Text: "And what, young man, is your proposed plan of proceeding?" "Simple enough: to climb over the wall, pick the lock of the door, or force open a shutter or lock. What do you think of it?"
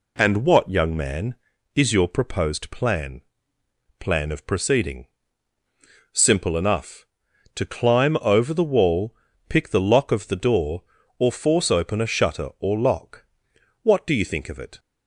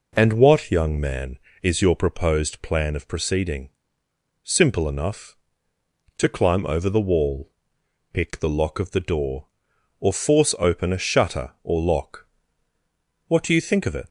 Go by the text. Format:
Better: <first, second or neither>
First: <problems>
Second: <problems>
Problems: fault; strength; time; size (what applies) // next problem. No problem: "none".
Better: second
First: says "plan" twice; at 3.9 s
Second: none